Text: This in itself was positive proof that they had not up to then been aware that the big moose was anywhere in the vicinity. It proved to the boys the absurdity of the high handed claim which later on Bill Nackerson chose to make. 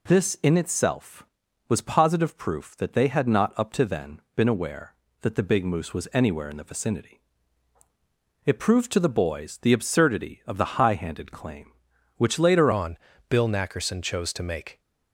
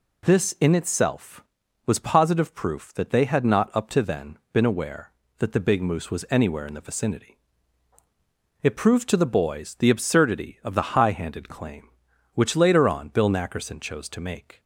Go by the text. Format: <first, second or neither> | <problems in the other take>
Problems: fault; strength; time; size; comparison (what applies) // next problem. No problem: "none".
second | pauses between "then" and "been"; slight; at 4.2 s; 0.16 s long; slight in the second // changes voice at "on"; from 12.7 s on; 2.0 s long // pauses between "on" and "Bill"; slight; at 12.9 s; 0.32 s long